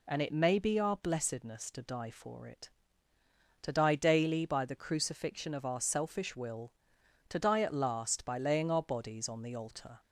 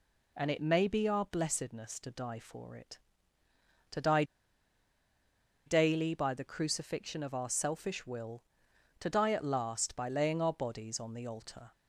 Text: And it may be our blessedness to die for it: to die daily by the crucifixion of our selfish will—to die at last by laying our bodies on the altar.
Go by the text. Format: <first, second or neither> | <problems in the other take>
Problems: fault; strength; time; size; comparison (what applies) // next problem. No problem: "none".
first | pauses between "die" and "daily"; strong; at 4.2 s; 1.4 s long